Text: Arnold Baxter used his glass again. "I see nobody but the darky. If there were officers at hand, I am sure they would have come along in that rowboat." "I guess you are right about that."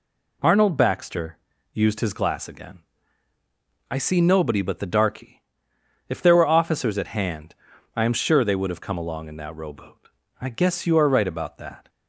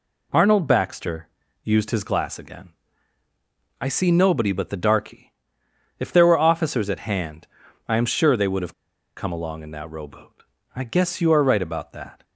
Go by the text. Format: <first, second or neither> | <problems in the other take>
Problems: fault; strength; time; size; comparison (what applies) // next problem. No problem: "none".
first | pauses between "Baxter" and "used"; slight; at 1.2 s; 0.36 s long; slight in the first // pauses between "have" and "come"; at 8.7 s; 0.45 s long